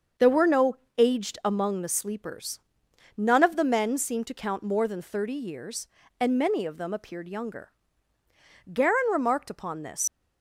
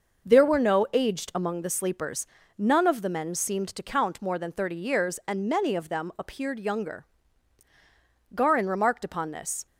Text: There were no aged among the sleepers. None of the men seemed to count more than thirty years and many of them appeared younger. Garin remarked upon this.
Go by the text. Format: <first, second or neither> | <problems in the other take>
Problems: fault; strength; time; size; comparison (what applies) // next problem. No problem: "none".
second | starts louder than the rest; until 1.3 s; 6.5 dB // pauses between "no" and "aged"; slight; at 0.7 s; 0.20 s long // leaves "this" unfinished; at 10.0 s; 115 ms